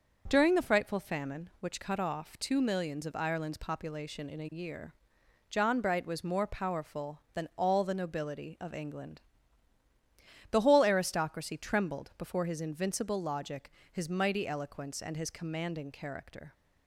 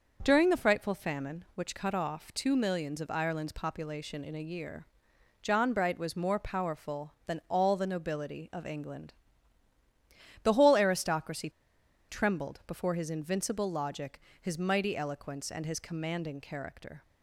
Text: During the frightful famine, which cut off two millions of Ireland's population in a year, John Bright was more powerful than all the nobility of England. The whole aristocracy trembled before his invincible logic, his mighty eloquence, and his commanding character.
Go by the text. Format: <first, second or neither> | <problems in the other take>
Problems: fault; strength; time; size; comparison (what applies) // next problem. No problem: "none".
first | starts louder than the rest; noticeable; until 1.2 s; 6 dB // pauses between "aristocracy" and "trembled"; noticeable; at 11.4 s; 0.59 s long